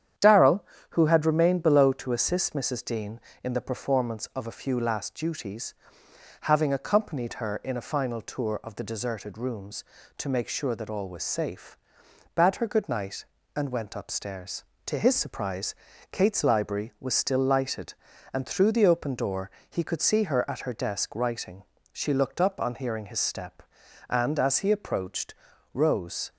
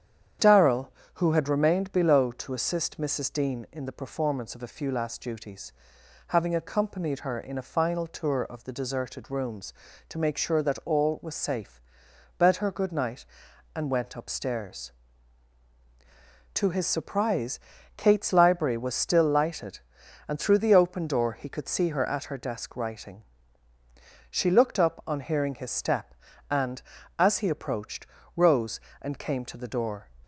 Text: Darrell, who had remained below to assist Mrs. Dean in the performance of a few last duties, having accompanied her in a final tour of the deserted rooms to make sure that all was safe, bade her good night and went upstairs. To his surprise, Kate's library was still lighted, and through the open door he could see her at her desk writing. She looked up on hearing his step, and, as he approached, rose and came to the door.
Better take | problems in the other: second | starts louder than the rest; strong; until 1.4 s; 9.5 dB; strong in the second // pauses between "door" and "he"; slight; at 19.5 s; 0.18 s long // stops before "and came to the door"; at 26.3 s

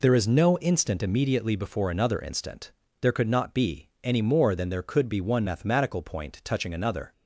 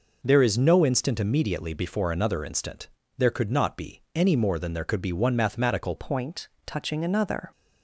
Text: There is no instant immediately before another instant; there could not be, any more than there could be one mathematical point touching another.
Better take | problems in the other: first | changes voice at "point"; from 5.9 s on; 1.6 s long // pauses between "point" and "touching"; slight; at 6.4 s; 0.16 s long

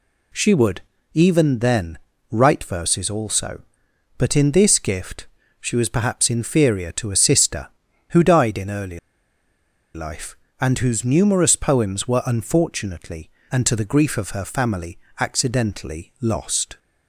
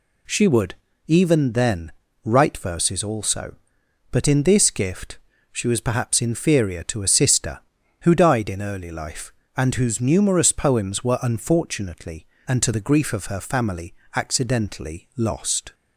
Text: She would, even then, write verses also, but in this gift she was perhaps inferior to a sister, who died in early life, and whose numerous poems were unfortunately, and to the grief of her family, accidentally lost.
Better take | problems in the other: second | pauses between "gift" and "she"; slight; at 5.2 s; 0.34 s long; slight in the second // pauses between "early" and "life"; noticeable; at 8.9 s; 0.95 s long

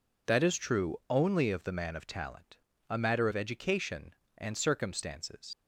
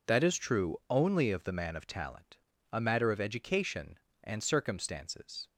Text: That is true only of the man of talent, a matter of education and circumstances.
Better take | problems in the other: second | leaves "circumstances" unfinished; at 5.5 s; 105 ms

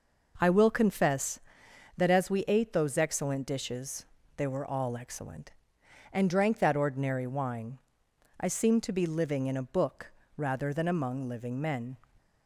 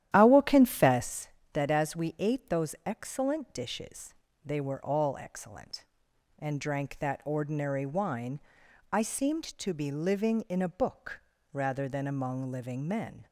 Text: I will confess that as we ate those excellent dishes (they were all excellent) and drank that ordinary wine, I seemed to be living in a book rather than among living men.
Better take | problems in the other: first | starts louder than the rest; strong; until 1.1 s; 12 dB // pauses between "book" and "rather"; slight; at 11.2 s; 0.32 s long; slight in the first

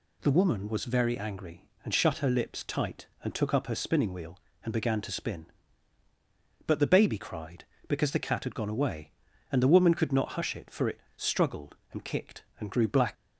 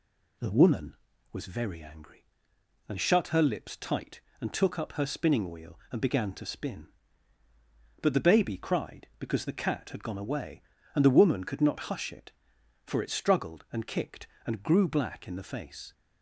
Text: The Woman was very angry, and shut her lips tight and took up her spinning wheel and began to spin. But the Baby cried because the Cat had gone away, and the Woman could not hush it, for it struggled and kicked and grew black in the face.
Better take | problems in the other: second | pauses between "it" and "struggled"; slight; at 10.9 s; 0.16 s long // stops before "in the face"; at 13.1 s

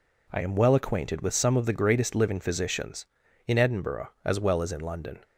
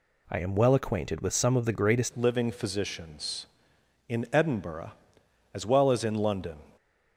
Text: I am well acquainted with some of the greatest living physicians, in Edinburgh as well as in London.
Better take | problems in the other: first | changes voice at "living"; from 2.1 s on; 4.4 s long

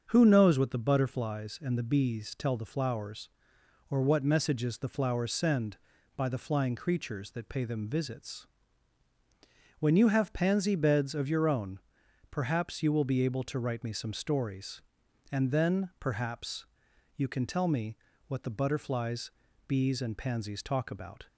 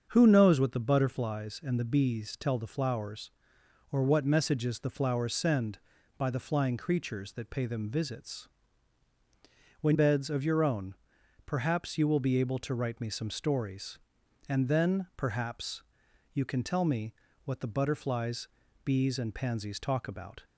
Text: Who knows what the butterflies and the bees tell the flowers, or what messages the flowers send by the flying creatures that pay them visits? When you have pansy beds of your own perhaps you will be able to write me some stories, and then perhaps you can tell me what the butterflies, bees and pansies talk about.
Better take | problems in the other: first | starts louder than the rest; until 1.1 s; 7 dB; also in the first // skips "you have pansy"; at 9.9 s // pauses between "own" and "perhaps"; noticeable; at 10.9 s; 0.50 s long; noticeable in the first // pauses between "perhaps" and "you"; noticeable; at 15.8 s; 0.50 s long; noticeable in the first // pauses between "me" and "what"; slight; at 17.1 s; 0.32 s long; slight in the first

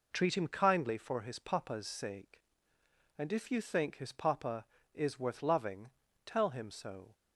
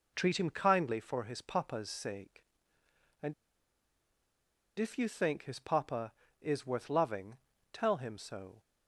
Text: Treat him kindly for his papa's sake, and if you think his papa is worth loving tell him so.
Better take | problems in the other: first | pauses between "and" and "if"; strong; at 3.3 s; 1.4 s long // pauses between "loving" and "tell"; slight; at 7.3 s; 0.36 s long; slight in the first

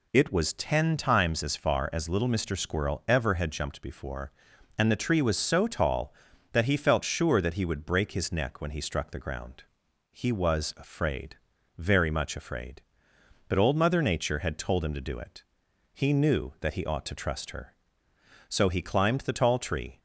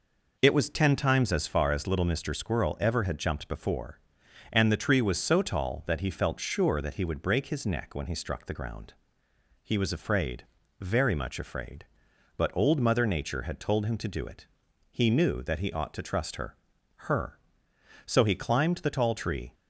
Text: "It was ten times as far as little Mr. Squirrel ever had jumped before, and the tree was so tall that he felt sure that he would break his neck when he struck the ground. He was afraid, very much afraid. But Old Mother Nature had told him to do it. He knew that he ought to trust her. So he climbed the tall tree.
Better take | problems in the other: first | says "her" twice; at 17.0 s

